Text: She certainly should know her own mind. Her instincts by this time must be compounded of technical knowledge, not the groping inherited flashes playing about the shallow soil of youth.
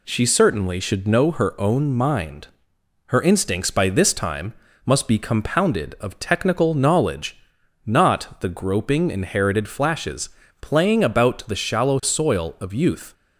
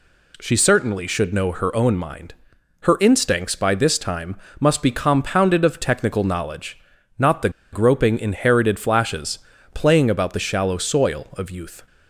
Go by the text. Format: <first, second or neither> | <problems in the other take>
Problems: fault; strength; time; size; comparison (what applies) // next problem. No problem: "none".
first | pauses between "time" and "must"; slight; at 4.3 s; 0.24 s long; slight in the first // pauses between "the" and "groping"; slight; at 7.4 s; 0.23 s long // pauses between "flashes" and "playing"; slight; at 9.3 s; 0.36 s long; slight in the first